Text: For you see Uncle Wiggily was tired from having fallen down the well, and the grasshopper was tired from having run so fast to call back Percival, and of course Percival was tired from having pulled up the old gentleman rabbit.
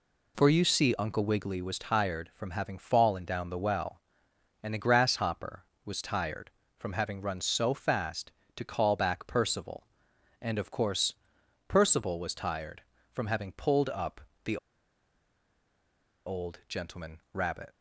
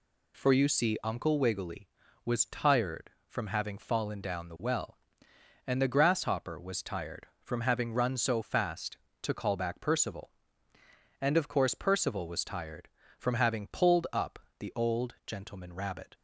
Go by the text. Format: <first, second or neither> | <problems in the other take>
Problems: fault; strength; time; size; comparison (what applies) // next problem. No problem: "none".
second | pauses between "course" and "Percival"; noticeable; at 11.1 s; 0.54 s long // pauses between "up" and "the"; slight; at 14.1 s; 0.24 s long; slight in the second // pauses between "the" and "old"; strong; at 14.5 s; 1.6 s long